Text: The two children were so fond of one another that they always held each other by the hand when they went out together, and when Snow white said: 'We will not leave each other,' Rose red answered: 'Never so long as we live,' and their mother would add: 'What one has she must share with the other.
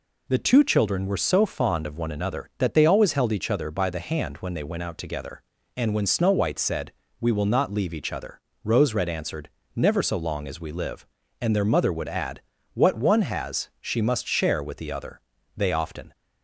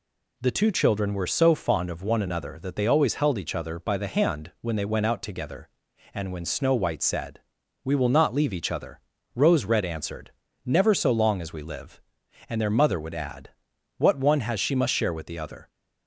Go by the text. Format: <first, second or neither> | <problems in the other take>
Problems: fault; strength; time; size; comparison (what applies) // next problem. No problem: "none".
second | goes on to say "They often"; from 15.5 s on; 0.60 s long